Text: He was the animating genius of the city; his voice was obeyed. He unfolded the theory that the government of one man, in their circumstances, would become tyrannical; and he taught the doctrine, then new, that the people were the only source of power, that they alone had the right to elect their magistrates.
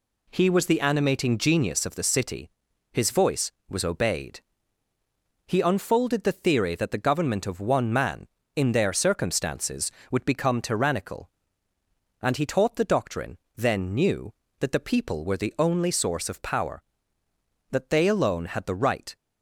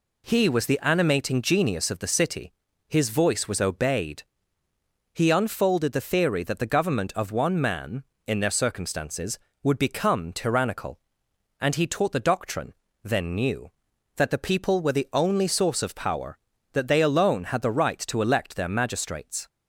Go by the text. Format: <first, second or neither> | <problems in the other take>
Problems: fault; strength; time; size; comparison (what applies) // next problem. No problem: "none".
second | stops before "to elect their magistrates"; at 19.1 s